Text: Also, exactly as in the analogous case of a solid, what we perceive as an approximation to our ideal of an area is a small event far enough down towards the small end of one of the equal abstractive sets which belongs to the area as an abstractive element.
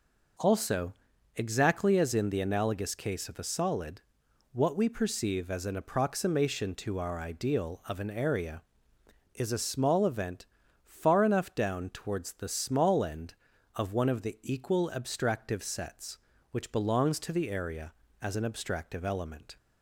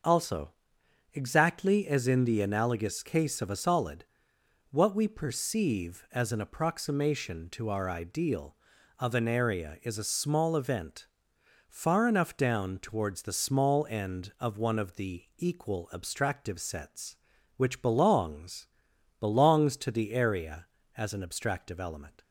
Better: first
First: pauses between "event" and "far"; at 10.4 s; 0.40 s long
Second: pauses between "event" and "far"; noticeable; at 11.0 s; 0.62 s long // pauses between "the" and "equal"; slight; at 15.2 s; 0.16 s long // says "belongs" twice; at 19.1 s

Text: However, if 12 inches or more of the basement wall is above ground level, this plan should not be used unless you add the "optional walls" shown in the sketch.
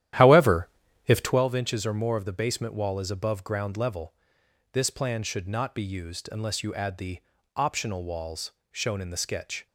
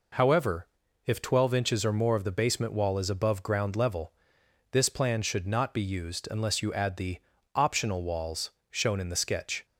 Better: second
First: starts louder than the rest; strong; until 1.4 s; 12 dB // pauses between "the" and "optional"; at 7.1 s; 0.38 s long // pauses between "walls" and "shown"; slight; at 8.5 s; 0.18 s long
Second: pauses between "the" and "optional"; at 7.1 s; 0.38 s long // pauses between "walls" and "shown"; slight; at 8.5 s; 0.18 s long

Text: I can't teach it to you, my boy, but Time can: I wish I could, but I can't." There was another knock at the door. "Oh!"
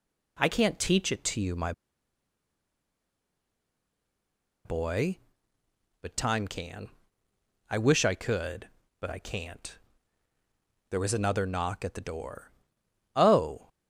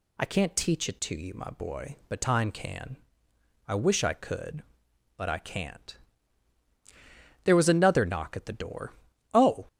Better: second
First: pauses between "my" and "boy"; strong; at 1.7 s; 2.9 s long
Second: none

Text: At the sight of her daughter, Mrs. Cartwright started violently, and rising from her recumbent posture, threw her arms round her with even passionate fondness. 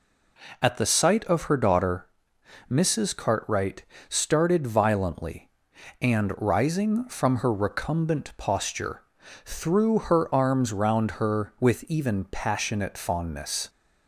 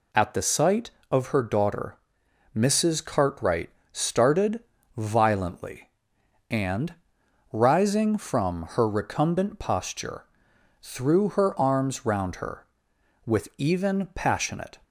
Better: first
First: pauses between "Cartwright" and "started"; slight; at 3.8 s; 0.24 s long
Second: pauses between "Cartwright" and "started"; slight; at 3.6 s; 0.22 s long // pauses between "started" and "violently"; slight; at 4.6 s; 0.34 s long // pauses between "and" and "rising"; noticeable; at 6.9 s; 0.58 s long // stops before "fondness"; at 14.8 s

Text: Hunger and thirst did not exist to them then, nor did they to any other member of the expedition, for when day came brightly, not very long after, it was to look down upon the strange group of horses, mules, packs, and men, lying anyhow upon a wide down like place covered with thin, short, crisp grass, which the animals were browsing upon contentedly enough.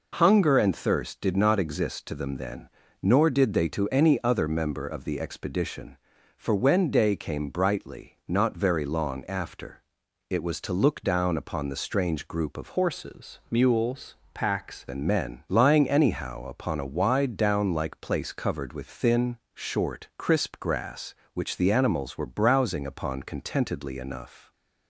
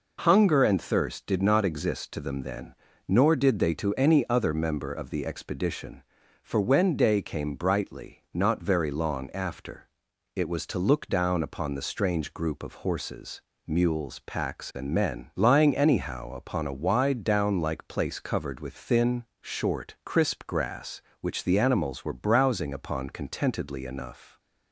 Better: second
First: changes voice from "horses" to "packs"; from 12.7 to 14.8 s; 2.1 s long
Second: none

